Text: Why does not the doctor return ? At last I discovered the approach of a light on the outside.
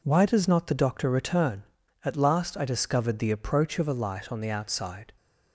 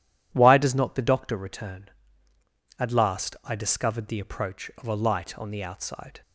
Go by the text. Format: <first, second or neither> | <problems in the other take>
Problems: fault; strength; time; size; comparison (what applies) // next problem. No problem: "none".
neither | none